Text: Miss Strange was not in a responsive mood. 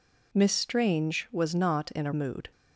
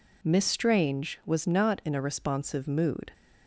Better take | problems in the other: second | skips "responsive"; at 2.1 s

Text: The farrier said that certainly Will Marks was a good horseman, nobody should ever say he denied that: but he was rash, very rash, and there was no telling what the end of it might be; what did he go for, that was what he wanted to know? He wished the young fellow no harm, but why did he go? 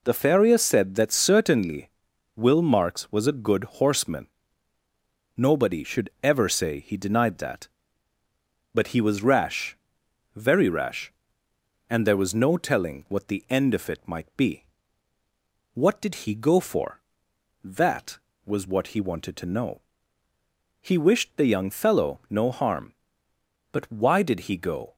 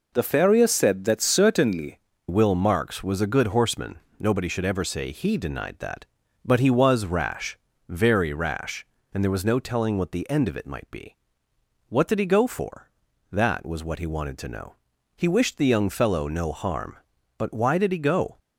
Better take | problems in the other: first | changes voice at "Will"; from 2.2 s on; 16.1 s long

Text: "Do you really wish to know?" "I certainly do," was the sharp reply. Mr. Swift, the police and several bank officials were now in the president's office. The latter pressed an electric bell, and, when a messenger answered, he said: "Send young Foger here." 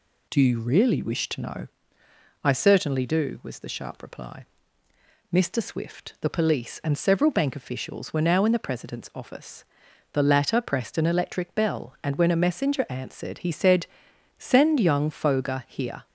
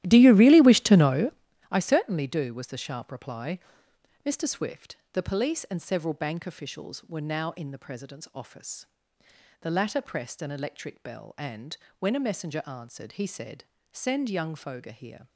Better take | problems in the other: first | starts louder than the rest; strong; until 1.5 s; 13.5 dB

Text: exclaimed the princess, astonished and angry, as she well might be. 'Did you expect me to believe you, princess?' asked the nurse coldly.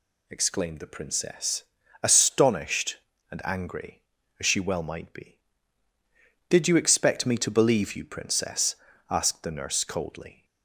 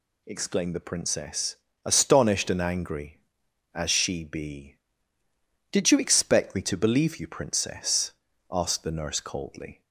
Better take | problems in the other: first | skips "well might"; at 4.2 s

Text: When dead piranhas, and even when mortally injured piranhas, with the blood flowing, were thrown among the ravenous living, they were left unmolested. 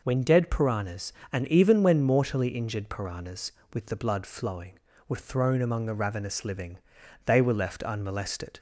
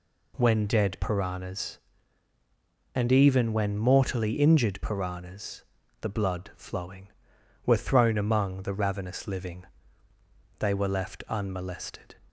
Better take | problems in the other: first | skips "with"; at 5.8 s

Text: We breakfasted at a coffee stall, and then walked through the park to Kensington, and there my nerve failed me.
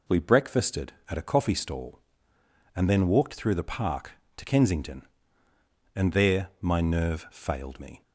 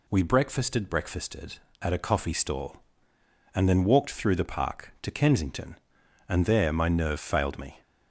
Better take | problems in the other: first | says "breakfasted" twice; at 0.8 s

